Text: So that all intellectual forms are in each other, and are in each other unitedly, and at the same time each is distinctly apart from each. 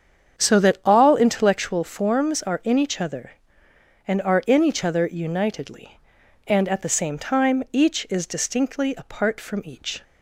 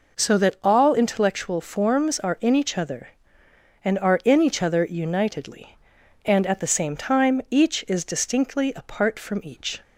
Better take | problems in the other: second | starts louder than the rest; strong; until 2.1 s; 8 dB

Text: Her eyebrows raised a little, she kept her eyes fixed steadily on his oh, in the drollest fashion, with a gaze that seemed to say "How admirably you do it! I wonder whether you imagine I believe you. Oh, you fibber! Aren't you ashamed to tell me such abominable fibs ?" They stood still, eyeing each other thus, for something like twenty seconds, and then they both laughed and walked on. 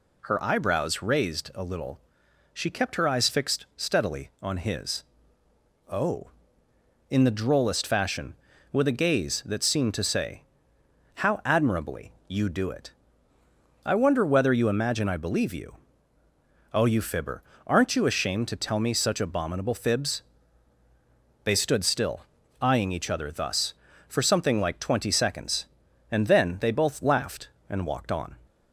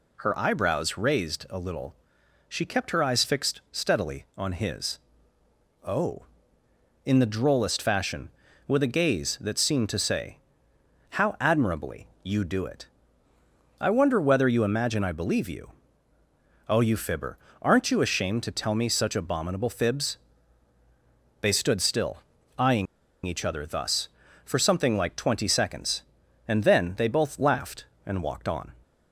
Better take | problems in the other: first | pauses between "his" and "oh"; noticeable; at 4.9 s; 0.86 s long; noticeable in the first // pauses between "say" and "How"; noticeable; at 10.3 s; 0.72 s long; noticeable in the first // pauses between "eyeing" and "each"; at 22.8 s; 0.40 s long

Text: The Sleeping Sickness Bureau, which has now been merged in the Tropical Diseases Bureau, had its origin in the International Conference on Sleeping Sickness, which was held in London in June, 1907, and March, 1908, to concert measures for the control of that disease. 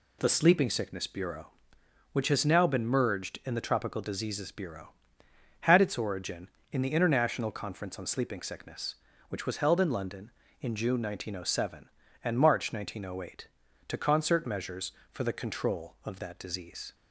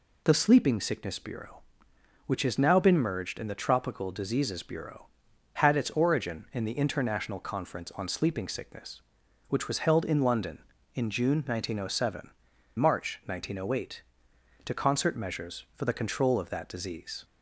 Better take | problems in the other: first | skips "and"; at 12.5 s

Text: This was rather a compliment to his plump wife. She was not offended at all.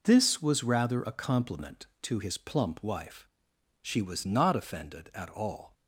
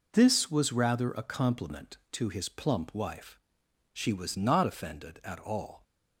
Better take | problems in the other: neither | none

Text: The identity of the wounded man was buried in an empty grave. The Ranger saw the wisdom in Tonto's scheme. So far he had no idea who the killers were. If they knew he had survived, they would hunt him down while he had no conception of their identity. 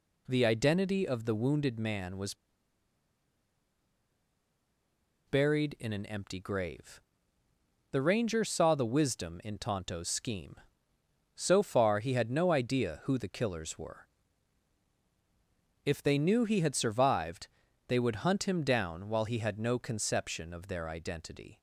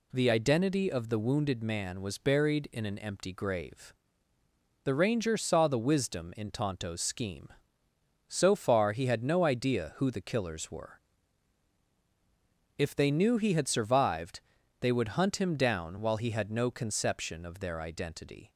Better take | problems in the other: second | pauses between "was" and "buried"; strong; at 2.3 s; 2.9 s long

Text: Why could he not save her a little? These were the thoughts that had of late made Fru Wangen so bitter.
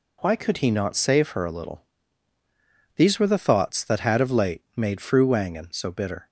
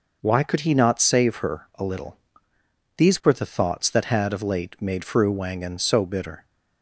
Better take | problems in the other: neither | none

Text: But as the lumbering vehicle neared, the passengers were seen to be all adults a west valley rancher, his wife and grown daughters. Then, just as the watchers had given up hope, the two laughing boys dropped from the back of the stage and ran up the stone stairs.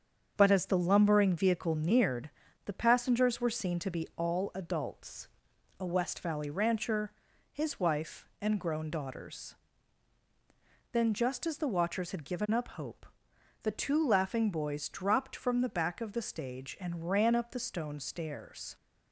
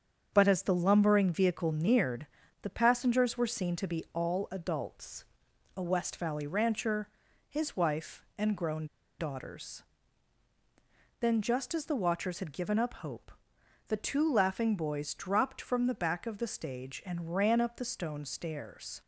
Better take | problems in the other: first | starts louder than the rest; until 1.3 s; 7 dB; also in the first // pauses between "adults" and "a"; noticeable; at 5.2 s; 0.52 s long; noticeable in the first // pauses between "grown" and "daughters"; slight; at 8.8 s; 0.33 s long

